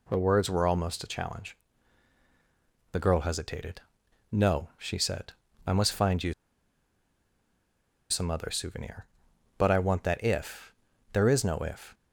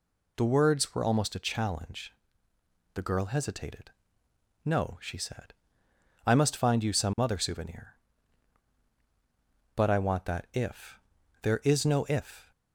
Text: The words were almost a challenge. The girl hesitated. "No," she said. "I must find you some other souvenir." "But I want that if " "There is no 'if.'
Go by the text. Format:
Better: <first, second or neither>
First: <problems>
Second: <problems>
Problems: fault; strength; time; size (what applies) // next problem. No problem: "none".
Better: second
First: pauses between "you" and "some"; strong; at 6.3 s; 1.7 s long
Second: none